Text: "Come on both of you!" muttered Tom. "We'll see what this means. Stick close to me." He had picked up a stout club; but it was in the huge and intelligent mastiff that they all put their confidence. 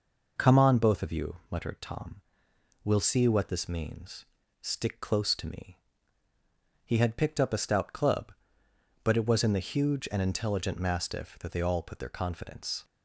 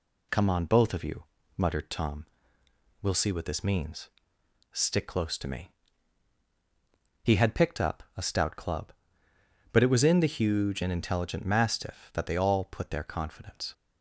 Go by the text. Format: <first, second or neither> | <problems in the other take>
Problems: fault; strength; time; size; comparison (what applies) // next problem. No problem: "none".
neither | none